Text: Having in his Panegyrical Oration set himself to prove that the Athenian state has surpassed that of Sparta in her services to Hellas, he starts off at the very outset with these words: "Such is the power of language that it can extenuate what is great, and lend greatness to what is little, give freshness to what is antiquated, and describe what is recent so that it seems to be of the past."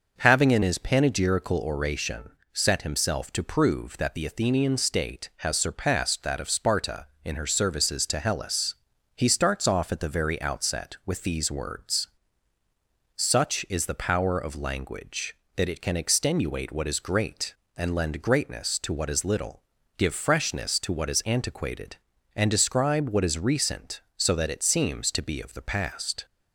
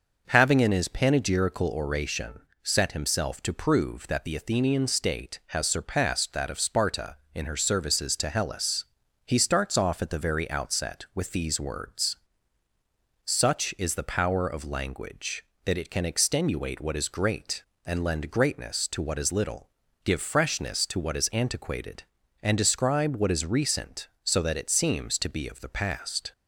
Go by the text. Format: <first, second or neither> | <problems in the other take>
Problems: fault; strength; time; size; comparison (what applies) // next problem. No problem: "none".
neither | pauses between "Oration" and "set"; slight; the same in both